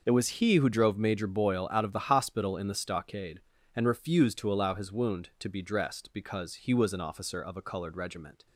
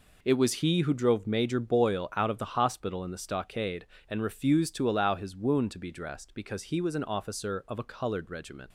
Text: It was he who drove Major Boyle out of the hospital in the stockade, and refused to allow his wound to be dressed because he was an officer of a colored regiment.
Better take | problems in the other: neither | none

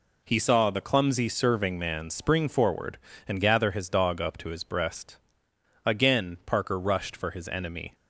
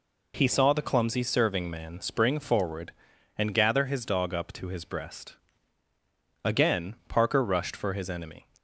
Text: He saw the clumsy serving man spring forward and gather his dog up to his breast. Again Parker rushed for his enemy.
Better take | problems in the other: neither | none

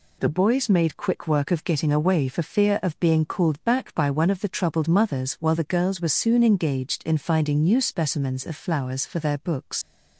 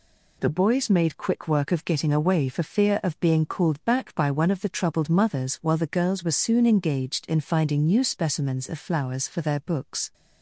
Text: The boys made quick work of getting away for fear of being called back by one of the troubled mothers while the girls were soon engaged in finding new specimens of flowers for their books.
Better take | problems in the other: second | leaves "books" unfinished; at 9.8 s; 95 ms

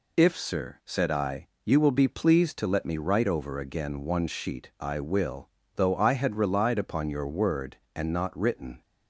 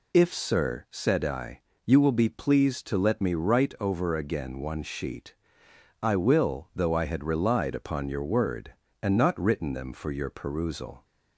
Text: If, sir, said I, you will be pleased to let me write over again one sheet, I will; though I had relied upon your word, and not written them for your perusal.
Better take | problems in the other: second | stops before "them for your perusal"; at 8.8 s

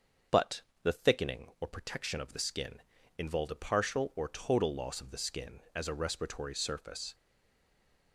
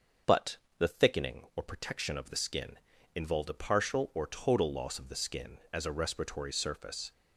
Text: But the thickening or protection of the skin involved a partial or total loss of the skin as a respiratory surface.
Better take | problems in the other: second | starts louder than the rest; until 1.6 s; 6.5 dB; also in the second // pauses between "But" and "the"; slight; at 0.6 s; 0.20 s long; slight in the second // pauses between "skin" and "involved"; at 2.7 s; 0.38 s long; also in the second // stays silent after the last word; from 7.1 s on; 1.0 s long

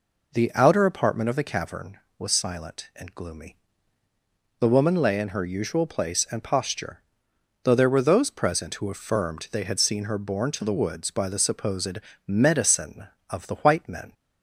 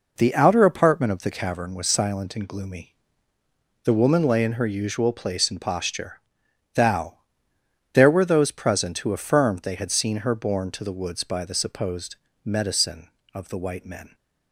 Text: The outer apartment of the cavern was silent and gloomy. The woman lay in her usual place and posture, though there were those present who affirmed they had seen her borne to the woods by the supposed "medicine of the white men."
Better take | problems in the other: first | says "thou" for "though"; at 6.7 s // pauses between "supposed" and "medicine"; slight; at 12.1 s; 0.30 s long; slight in the first

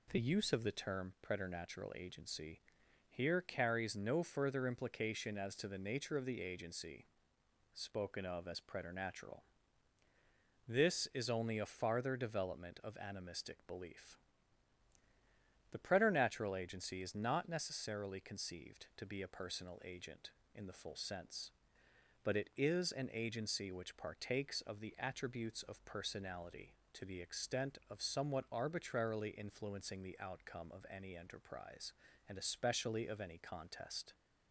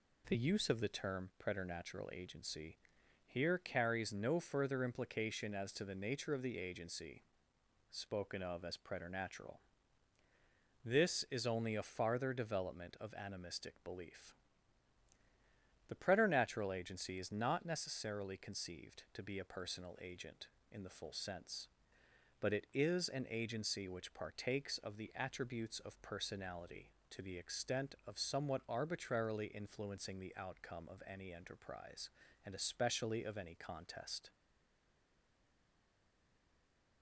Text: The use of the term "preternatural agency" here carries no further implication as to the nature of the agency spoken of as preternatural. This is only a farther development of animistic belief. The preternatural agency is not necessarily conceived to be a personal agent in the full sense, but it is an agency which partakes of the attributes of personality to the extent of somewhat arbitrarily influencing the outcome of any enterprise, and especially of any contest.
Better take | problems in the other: first | pauses between "agency" and "here"; noticeable; at 2.7 s; 0.50 s long; noticeable in the first // pauses between "agency" and "spoken"; noticeable; at 7.2 s; 0.70 s long; noticeable in the first // stays silent after the last word; strong; from 34.3 s on; 2.7 s long

